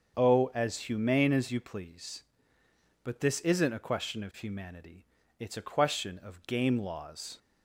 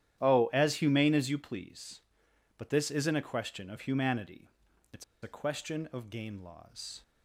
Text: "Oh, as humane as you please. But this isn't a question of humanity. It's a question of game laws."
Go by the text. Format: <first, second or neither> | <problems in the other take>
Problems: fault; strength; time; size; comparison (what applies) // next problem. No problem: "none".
first | starts louder than the rest; strong; until 1.2 s; 11 dB; also in the first // pauses between "It's" and "a"; slight; at 5.0 s; 0.20 s long